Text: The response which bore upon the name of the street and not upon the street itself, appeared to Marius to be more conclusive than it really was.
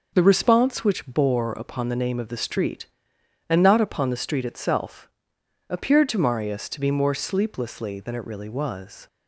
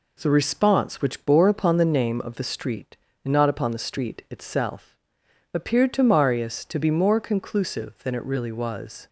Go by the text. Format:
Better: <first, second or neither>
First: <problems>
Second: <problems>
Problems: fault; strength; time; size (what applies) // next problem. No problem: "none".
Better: second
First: says "sleeplessly" for "conclusive"; at 7.1 s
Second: none